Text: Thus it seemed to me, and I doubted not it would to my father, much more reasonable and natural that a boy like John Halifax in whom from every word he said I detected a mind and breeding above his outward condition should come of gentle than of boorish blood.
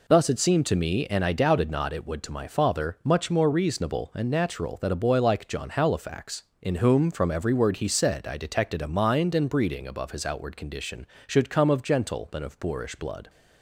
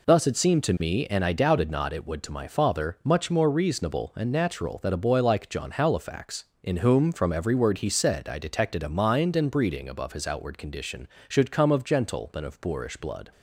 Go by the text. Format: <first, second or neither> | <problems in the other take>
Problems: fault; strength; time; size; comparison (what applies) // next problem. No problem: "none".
neither | none